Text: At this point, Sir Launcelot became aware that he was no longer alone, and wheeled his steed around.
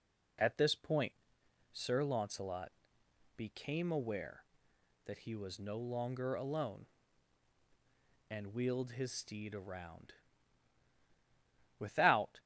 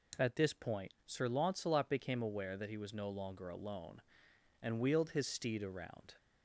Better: second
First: pauses between "Launcelot" and "became"; noticeable; at 2.6 s; 0.66 s long // goes on to say "Without"; noticeable; from 11.7 s on; 0.62 s long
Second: none

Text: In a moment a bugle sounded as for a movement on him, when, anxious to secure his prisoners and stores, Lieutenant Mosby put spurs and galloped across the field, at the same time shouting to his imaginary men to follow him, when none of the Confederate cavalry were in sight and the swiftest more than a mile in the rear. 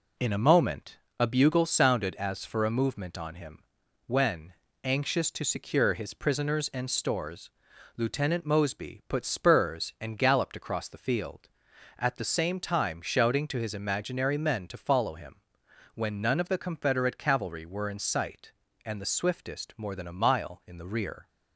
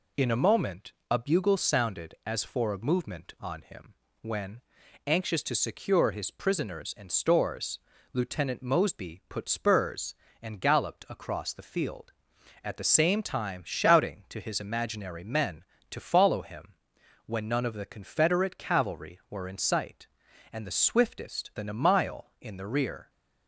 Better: first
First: pauses between "moment" and "a"; slight; at 0.9 s; 0.22 s long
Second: pauses between "moment" and "a"; slight; at 0.9 s; 0.18 s long // skips "more"; at 21.5 s

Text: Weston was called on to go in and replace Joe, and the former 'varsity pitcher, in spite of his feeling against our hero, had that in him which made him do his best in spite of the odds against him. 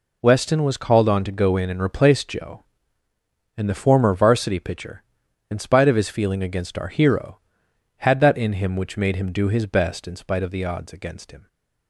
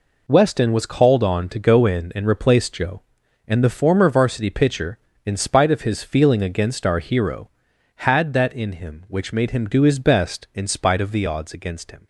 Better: neither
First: none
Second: none

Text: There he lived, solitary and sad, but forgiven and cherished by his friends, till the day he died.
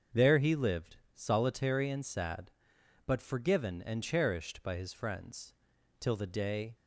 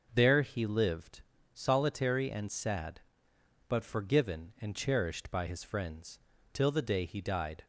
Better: second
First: starts louder than the rest; until 1.3 s; 6.5 dB // stops before "he died"; at 6.7 s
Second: none

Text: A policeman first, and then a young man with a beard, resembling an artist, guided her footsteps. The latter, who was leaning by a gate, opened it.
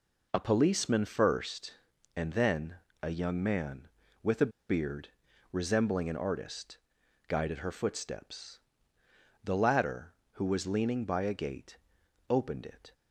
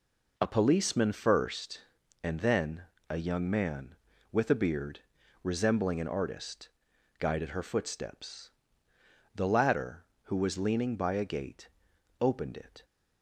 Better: second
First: pauses between "then" and "a"; slight; at 2.7 s; 0.26 s long // pauses between "a" and "beard"; slight; at 4.5 s; 0.18 s long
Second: pauses between "then" and "a"; slight; at 2.8 s; 0.26 s long

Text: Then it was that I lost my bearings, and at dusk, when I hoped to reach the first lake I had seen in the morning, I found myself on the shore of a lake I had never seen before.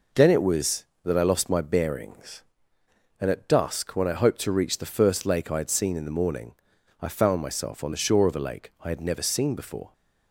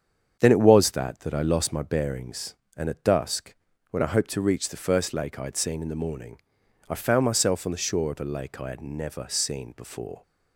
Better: first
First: none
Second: starts louder than the rest; strong; until 1.4 s; 7.5 dB // says "that" twice; at 1.1 s

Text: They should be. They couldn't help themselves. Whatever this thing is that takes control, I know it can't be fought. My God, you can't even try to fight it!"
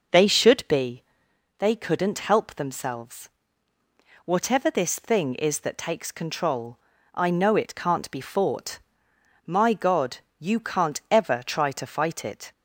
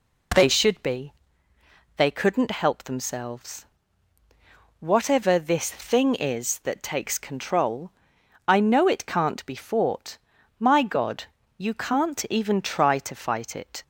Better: second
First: says "ever" for "even"; at 11.0 s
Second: none

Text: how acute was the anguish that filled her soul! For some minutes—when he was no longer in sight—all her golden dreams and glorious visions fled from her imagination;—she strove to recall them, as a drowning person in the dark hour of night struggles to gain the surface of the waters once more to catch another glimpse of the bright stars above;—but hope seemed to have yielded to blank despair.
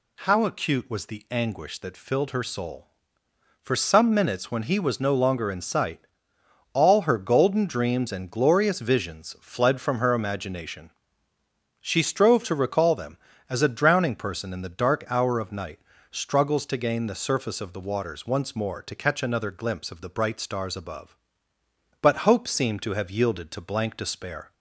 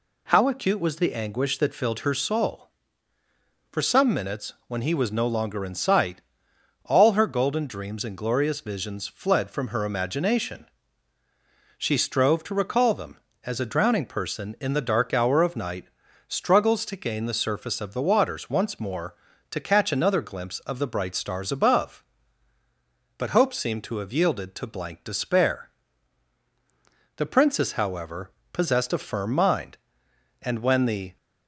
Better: first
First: pauses between "night" and "struggles"; slight; at 15.8 s; 0.32 s long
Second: pauses between "night" and "struggles"; at 15.8 s; 0.42 s long // goes on to say "The Princess however possessed a firm mind and when the"; strong; from 27.1 s on; 4.0 s long

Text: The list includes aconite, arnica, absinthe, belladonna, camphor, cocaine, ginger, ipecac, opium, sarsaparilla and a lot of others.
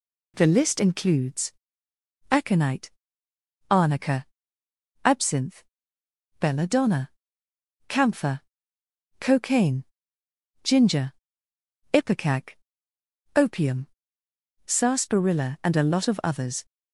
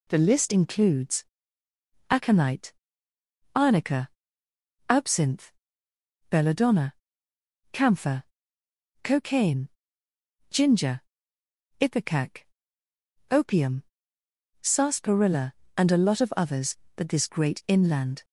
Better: first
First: pauses between "includes" and "aconite"; noticeable; at 1.5 s; 0.78 s long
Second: pauses between "includes" and "aconite"; noticeable; at 1.2 s; 0.86 s long // goes on to say "But this great inland"; noticeable; from 16.9 s on; 1.2 s long

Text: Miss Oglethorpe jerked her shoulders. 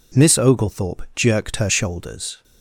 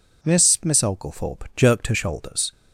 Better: first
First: none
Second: says "Miss" twice; at 0.6 s

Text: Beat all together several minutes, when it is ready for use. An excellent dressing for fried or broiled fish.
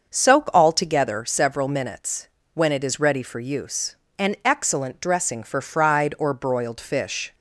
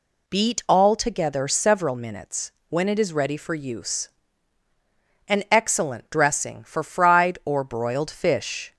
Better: second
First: starts louder than the rest; until 1.1 s; 6.5 dB // says "Soak" for "Beat"; at 0.1 s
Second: none

